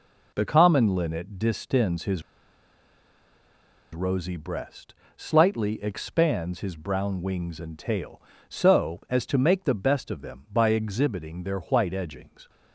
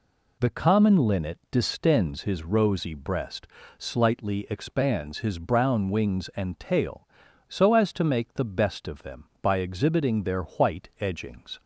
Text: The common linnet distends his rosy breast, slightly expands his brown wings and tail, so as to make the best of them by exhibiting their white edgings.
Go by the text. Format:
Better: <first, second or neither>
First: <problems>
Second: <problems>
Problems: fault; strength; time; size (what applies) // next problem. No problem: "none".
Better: second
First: pauses between "his" and "rosy"; strong; at 2.2 s; 1.7 s long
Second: none